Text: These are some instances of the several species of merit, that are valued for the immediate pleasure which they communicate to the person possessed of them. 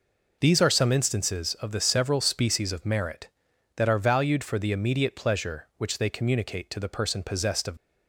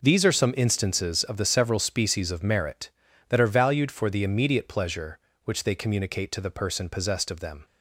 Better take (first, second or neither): second